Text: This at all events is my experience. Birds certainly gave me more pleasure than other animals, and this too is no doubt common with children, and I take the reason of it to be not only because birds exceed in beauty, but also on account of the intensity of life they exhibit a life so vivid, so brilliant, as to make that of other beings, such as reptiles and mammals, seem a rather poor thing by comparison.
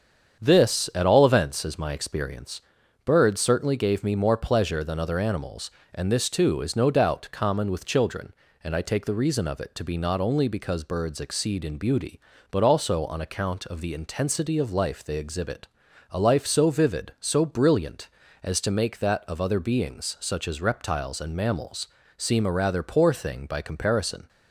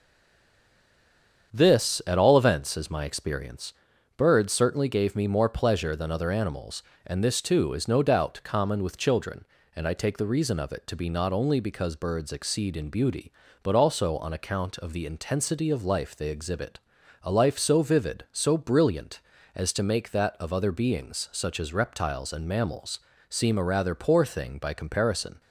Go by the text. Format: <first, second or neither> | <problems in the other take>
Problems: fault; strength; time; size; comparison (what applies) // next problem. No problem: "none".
first | stays silent before the first word; noticeable; until 1.5 s; 1.5 s long // starts louder than the rest; strong; until 2.5 s; 7.5 dB; strong in the first // pauses between "exhibit" and "a"; at 16.7 s; 0.44 s long; also in the first